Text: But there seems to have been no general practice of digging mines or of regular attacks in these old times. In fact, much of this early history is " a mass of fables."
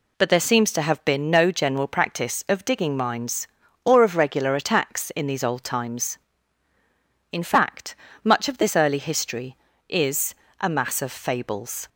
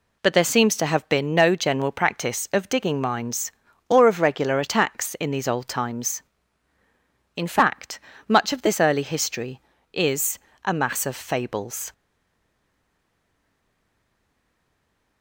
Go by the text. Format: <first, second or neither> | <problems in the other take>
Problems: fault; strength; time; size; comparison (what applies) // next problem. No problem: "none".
first | stays silent after the last word; strong; from 11.9 s on; 3.3 s long